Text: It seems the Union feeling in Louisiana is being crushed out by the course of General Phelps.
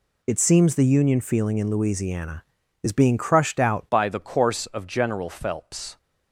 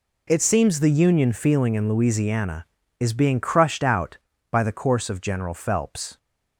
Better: second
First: changes voice at "by"; from 3.8 s on; 2.1 s long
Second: none

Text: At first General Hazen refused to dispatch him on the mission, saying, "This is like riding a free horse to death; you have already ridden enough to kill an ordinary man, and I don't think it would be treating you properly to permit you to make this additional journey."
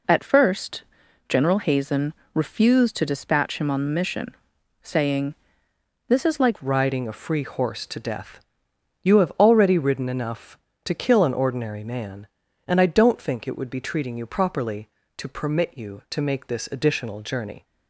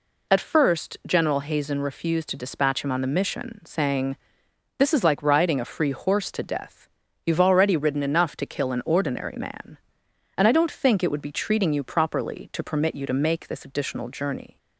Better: second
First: pauses between "first" and "General"; noticeable; at 0.8 s; 0.46 s long // pauses between "Hazen" and "refused"; slight; at 2.1 s; 0.22 s long // changes voice at "riding"; from 6.6 s on; 11.0 s long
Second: none

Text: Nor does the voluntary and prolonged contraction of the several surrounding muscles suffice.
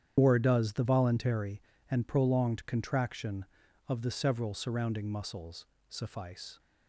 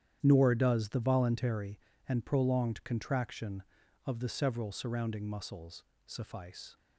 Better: second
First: loses the start of "Nor"; at 0.1 s; 115 ms // starts louder than the rest; strong; until 1.1 s; 9.5 dB // pauses between "muscles" and "suffice"; slight; at 5.6 s; 0.22 s long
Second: starts louder than the rest; strong; until 1.2 s; 10 dB // pauses between "muscles" and "suffice"; slight; at 5.8 s; 0.21 s long

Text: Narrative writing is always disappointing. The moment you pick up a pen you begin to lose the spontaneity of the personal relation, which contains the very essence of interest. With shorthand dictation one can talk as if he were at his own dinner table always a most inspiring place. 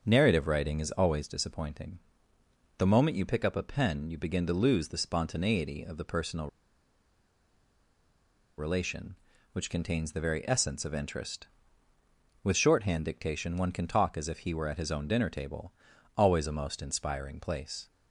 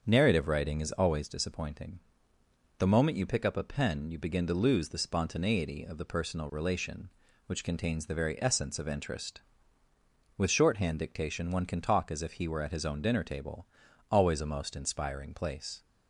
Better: second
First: starts louder than the rest; until 1.0 s; 7 dB // pauses between "personal" and "relation"; strong; at 6.4 s; 2.1 s long // pauses between "table" and "always"; at 15.7 s; 0.44 s long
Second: starts louder than the rest; until 1.0 s; 7 dB // pauses between "table" and "always"; at 13.6 s; 0.44 s long

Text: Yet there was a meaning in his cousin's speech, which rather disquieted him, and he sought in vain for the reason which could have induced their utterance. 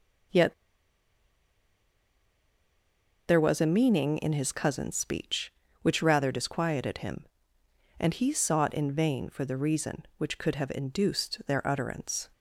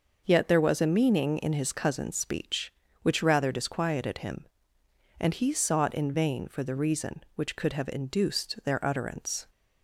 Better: second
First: pauses between "Yet" and "there"; strong; at 0.5 s; 2.7 s long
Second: none

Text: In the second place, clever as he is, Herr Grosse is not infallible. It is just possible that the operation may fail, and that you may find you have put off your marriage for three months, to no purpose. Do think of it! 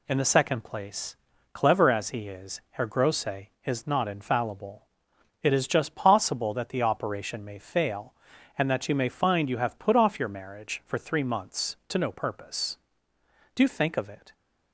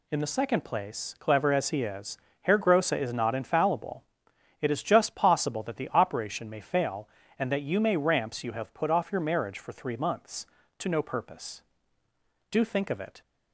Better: first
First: none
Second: says "ramps" for "find"; at 7.9 s

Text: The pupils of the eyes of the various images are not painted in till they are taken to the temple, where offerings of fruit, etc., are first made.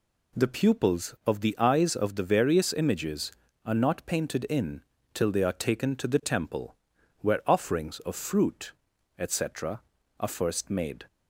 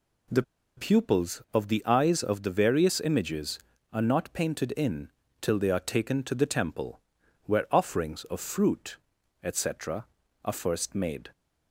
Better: first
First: pauses between "in" and "till"; slight; at 4.8 s; 0.32 s long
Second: pauses between "The" and "pupils"; slight; at 0.4 s; 0.34 s long // pauses between "in" and "till"; slight; at 5.0 s; 0.32 s long

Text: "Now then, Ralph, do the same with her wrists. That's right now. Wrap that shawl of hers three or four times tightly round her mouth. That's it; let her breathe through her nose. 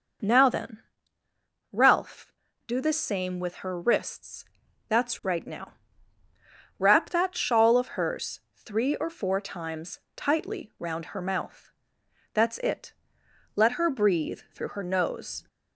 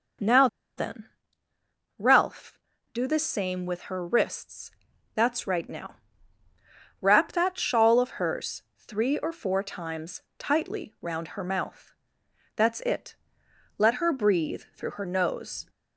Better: first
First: pauses between "times" and "tightly"; slight; at 9.9 s; 0.16 s long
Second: pauses between "Now" and "then"; slight; at 0.4 s; 0.29 s long // pauses between "times" and "tightly"; slight; at 10.2 s; 0.16 s long

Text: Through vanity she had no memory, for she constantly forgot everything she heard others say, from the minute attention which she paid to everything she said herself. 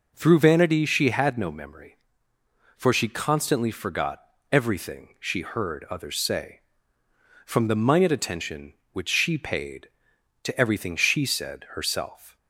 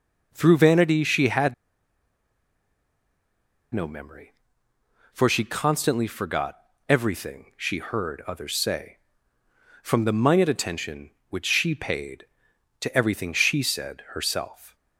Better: first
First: pauses between "forgot" and "everything"; slight; at 4.2 s; 0.29 s long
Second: pauses between "had" and "no"; strong; at 1.5 s; 2.1 s long // pauses between "forgot" and "everything"; slight; at 6.5 s; 0.30 s long

